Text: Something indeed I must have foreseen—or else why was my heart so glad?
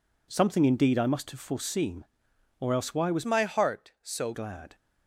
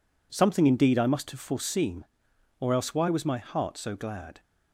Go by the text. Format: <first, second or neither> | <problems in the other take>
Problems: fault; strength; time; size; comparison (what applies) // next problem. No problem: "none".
second | changes voice from "my" to "so"; from 3.2 to 4.3 s; 1.1 s long